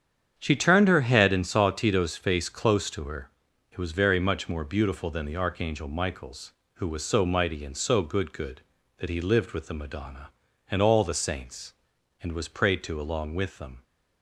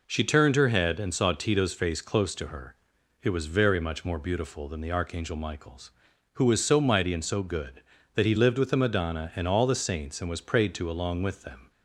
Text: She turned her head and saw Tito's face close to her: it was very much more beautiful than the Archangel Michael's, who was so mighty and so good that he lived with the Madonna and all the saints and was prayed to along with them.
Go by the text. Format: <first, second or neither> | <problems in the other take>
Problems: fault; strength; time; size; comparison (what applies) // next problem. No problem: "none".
second | starts louder than the rest; strong; until 1.3 s; 8 dB // says "good" twice; at 8.3 s